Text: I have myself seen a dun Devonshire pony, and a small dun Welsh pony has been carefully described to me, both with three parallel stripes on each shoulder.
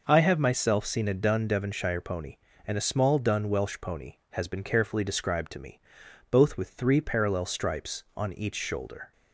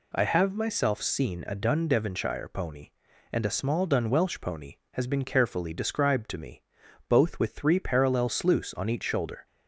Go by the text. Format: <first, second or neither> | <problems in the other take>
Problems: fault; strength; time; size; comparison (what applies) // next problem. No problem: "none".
first | says "sluice" for "stripes"; at 8.2 s